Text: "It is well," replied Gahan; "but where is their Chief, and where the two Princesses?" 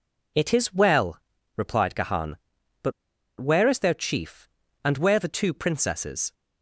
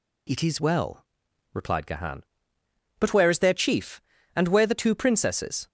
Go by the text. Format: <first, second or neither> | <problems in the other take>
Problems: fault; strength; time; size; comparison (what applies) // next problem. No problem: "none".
second | pauses between "but" and "where"; noticeable; at 2.9 s; 0.46 s long